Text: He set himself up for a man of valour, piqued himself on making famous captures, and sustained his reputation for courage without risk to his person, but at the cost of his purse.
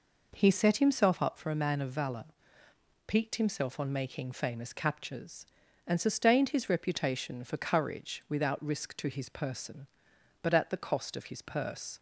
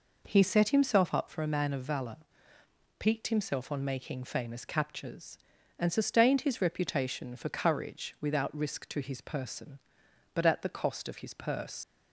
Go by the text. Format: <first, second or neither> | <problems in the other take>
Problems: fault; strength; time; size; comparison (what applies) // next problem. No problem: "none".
first | leaves "purse" unfinished; at 11.8 s; 65 ms